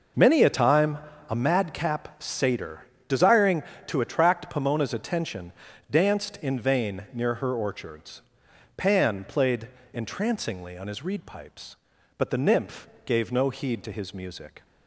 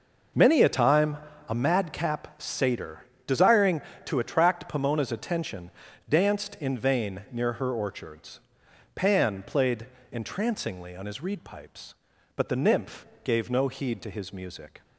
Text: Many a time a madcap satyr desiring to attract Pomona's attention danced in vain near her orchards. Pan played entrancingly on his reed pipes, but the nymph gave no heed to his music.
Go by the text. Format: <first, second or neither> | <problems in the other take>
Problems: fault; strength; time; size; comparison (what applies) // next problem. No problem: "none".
neither | pauses between "time" and "a"; slight; the same in both // pauses between "satyr" and "desiring"; slight; the same in both // pauses between "attention" and "danced"; the same in both // pauses between "played" and "entrancingly"; slight; the same in both // pauses between "nymph" and "gave"; slight; the same in both